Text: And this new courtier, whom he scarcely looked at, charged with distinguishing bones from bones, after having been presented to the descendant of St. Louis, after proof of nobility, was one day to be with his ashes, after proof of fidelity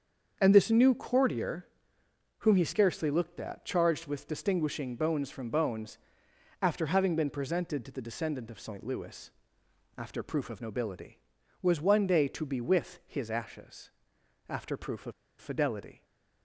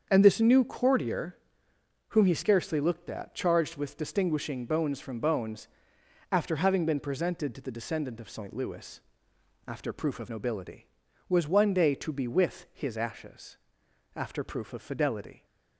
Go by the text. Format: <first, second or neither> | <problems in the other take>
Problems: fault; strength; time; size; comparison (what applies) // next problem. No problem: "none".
second | starts louder than the rest; until 1.4 s; 7 dB; also in the second // pauses between "of" and "fidelity"; slight; at 15.1 s; 0.26 s long // stays silent after the last word; slight; from 15.9 s on; 0.5 s long